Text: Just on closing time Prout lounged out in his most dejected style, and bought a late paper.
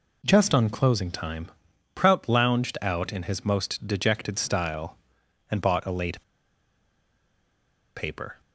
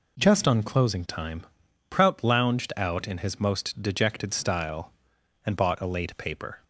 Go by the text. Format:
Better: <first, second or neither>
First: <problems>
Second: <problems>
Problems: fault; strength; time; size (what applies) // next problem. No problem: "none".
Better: second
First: pauses between "time" and "Prout"; at 1.4 s; 0.44 s long // pauses between "late" and "paper"; strong; at 6.2 s; 1.7 s long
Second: pauses between "time" and "Prout"; at 1.4 s; 0.44 s long